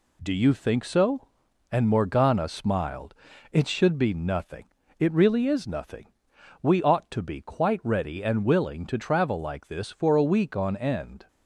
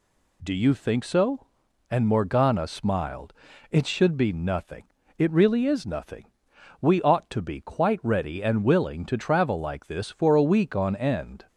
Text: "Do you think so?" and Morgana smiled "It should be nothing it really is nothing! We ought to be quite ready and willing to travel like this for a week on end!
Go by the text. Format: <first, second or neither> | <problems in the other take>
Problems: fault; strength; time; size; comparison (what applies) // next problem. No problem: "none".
second | gets quieter; noticeable; throughout; 4 dB // pauses between "smiled" and "It"; at 3.1 s; 0.38 s long; also in the second // pauses between "nothing" and "it"; slight; at 4.6 s; 0.32 s long; slight in the second